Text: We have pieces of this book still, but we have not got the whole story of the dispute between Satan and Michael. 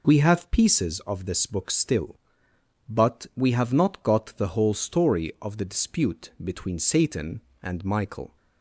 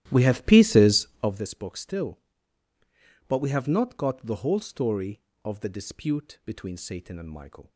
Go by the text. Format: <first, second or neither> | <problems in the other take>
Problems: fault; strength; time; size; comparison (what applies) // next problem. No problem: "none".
first | starts louder than the rest; strong; until 1.4 s; 13 dB